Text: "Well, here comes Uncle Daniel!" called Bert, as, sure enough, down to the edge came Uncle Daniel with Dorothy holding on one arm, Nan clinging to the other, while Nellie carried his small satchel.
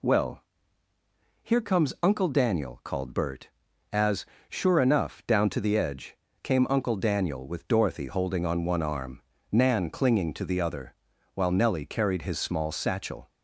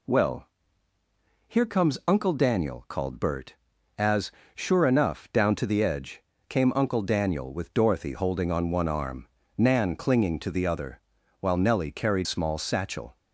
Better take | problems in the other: first | pauses between "edge" and "came"; slight; at 6.2 s; 0.26 s long; slight in the first // skips "his"; at 12.2 s

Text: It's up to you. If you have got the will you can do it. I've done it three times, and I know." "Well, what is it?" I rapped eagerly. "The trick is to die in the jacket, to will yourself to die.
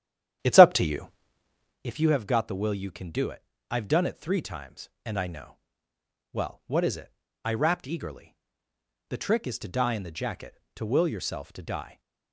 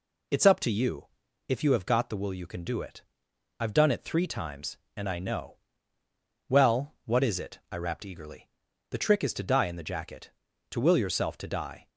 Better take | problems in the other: second | starts louder than the rest; strong; until 1.8 s; 11 dB

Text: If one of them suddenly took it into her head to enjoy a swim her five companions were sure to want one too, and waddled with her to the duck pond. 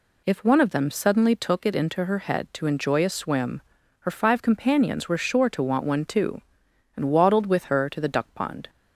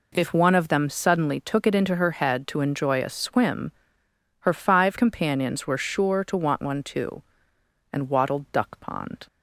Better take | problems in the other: first | pauses between "swim" and "her"; noticeable; at 3.7 s; 0.68 s long; also in the first // skips "with her to the"; at 8.5 s

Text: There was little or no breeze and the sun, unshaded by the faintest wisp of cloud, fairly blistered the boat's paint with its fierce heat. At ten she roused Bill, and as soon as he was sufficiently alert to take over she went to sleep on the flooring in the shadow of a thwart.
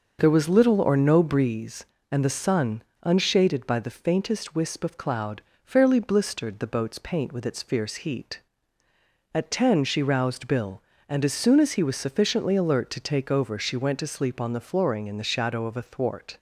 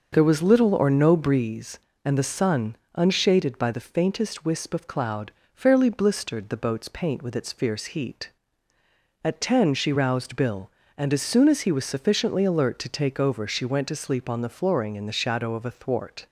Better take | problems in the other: neither | starts louder than the rest; the same in both

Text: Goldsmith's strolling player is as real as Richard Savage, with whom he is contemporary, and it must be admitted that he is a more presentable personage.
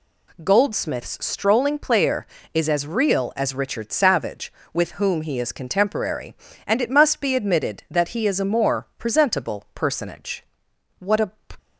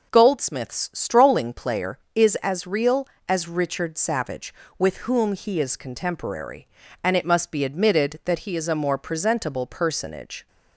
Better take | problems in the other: second | goes on to say "What a"; slight; from 10.9 s on; 0.32 s long

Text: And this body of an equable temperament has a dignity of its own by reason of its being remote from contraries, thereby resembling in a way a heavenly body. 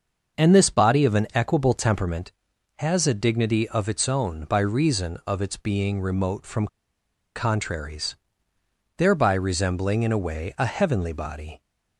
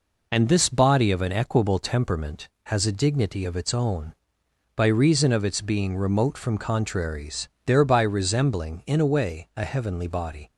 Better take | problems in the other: second | starts louder than the rest; until 1.4 s; 6.5 dB // pauses between "from" and "contraries"; noticeable; at 6.6 s; 0.68 s long

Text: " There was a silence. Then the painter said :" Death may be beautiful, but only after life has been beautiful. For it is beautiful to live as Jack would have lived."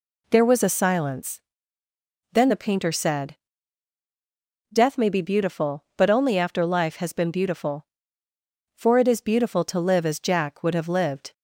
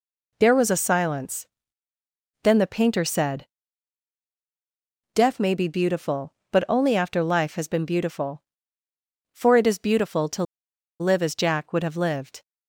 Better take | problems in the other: first | pauses between "to" and "live"; noticeable; at 10.4 s; 0.57 s long

